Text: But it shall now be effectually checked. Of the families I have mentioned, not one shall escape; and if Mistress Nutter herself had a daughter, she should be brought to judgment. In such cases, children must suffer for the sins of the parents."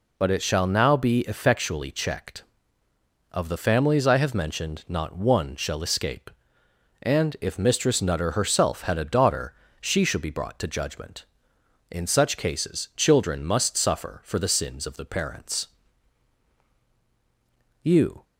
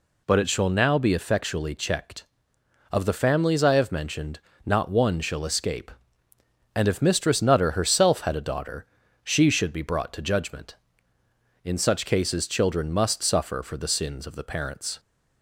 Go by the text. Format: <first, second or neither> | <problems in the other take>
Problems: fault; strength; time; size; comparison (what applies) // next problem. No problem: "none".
second | goes on to say "You"; slight; from 17.8 s on; 0.42 s long